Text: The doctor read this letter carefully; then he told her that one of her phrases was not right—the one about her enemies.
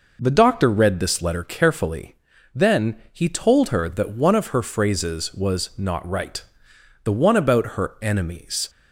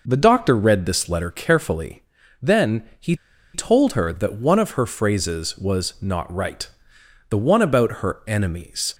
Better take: first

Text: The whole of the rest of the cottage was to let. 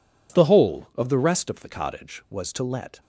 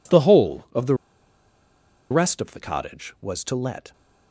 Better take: first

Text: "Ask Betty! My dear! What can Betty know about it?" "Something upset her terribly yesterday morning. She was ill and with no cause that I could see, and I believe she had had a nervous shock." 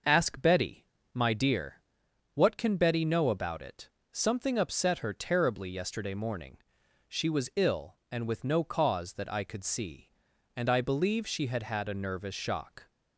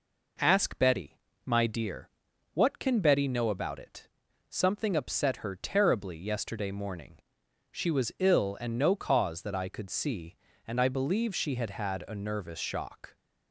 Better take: first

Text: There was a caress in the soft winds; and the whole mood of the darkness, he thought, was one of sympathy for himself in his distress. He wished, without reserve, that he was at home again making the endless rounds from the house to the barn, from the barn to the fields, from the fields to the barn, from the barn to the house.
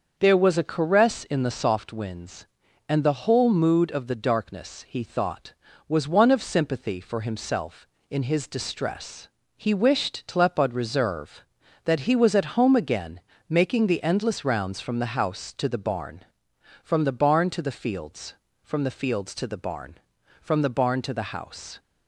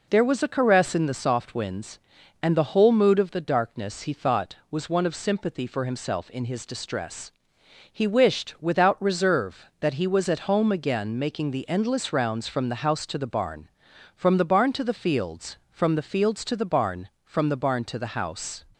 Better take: second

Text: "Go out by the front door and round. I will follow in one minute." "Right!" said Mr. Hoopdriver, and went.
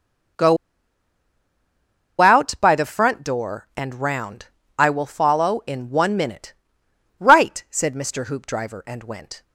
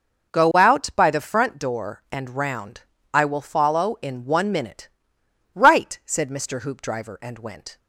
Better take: second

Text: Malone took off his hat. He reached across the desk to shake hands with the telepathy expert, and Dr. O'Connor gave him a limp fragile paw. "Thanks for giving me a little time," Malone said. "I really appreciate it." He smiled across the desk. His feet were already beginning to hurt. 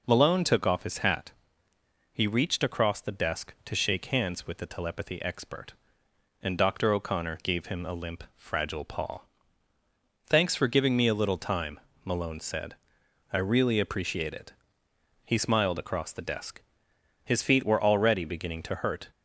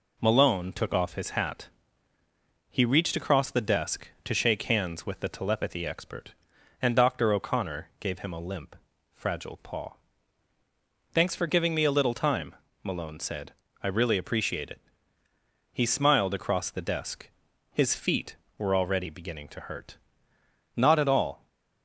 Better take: first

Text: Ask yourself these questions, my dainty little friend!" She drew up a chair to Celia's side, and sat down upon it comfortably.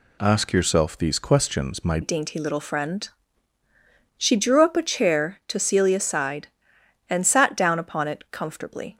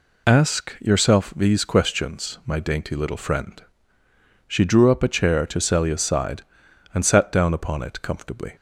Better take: second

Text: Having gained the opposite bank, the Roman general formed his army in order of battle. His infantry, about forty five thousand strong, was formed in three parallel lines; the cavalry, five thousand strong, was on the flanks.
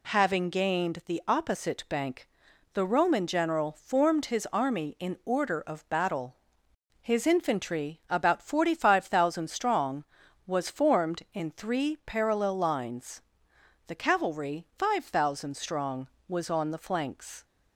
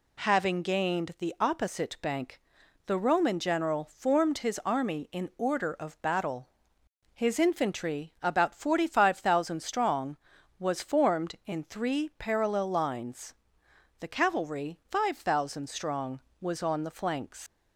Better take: first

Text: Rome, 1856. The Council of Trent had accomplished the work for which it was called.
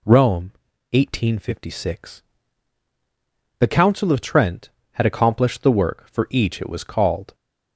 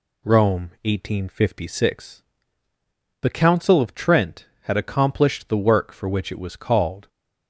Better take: second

